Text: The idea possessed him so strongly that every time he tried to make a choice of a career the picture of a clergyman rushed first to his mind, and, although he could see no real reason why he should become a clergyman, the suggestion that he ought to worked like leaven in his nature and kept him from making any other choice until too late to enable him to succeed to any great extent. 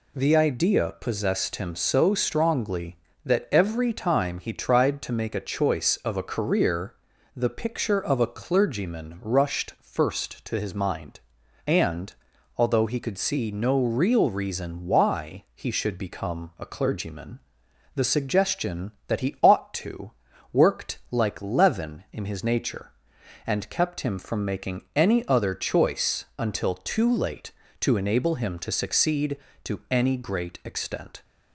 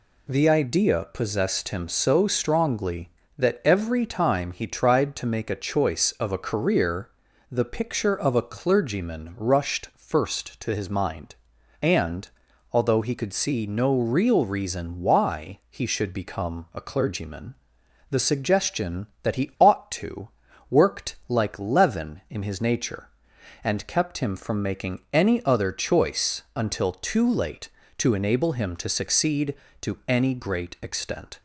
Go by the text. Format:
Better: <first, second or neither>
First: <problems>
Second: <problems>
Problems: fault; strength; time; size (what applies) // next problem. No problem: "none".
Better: neither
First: pauses between "career" and "the"; at 6.9 s; 0.42 s long // pauses between "to" and "worked"; at 20.1 s; 0.40 s long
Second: pauses between "career" and "the"; at 7.0 s; 0.42 s long // pauses between "to" and "worked"; at 20.2 s; 0.40 s long